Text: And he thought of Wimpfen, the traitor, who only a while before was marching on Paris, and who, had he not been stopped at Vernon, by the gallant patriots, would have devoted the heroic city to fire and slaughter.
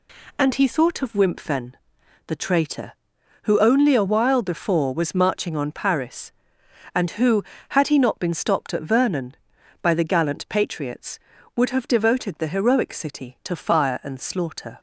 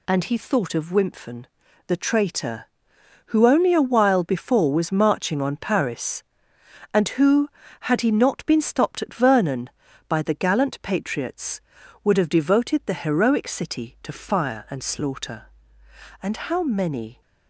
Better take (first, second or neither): first